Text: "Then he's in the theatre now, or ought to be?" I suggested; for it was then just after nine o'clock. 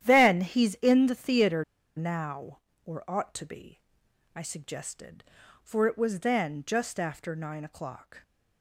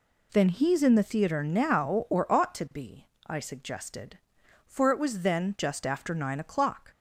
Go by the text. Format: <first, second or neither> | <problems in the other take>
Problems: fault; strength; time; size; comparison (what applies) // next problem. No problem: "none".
second | starts louder than the rest; strong; until 1.0 s; 11 dB // pauses between "theatre" and "now"; slight; at 1.6 s; 0.32 s long